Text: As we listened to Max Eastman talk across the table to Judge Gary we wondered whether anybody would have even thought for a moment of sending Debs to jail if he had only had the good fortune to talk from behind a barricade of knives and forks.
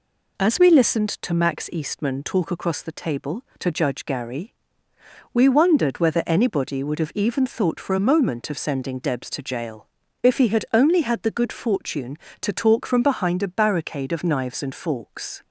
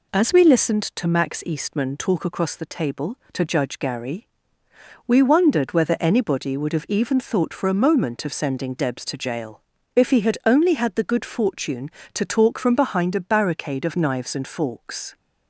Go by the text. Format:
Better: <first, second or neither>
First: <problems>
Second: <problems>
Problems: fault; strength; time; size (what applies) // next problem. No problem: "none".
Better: neither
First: pauses between "Gary" and "we"; noticeable; at 4.5 s; 0.78 s long // pauses between "jail" and "if"; at 9.8 s; 0.38 s long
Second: pauses between "Gary" and "we"; noticeable; at 4.2 s; 0.78 s long // pauses between "jail" and "if"; at 9.6 s; 0.36 s long